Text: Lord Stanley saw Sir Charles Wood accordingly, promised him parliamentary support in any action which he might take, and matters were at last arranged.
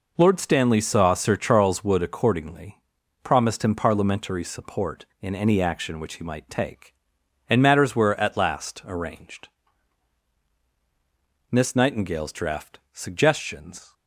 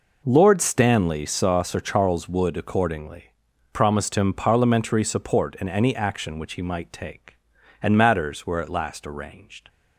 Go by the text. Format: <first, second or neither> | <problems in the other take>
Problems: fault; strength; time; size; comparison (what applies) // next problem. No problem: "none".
second | goes on to say "Miss Nightingale's draft Suggestions"; strong; from 11.5 s on; 2.4 s long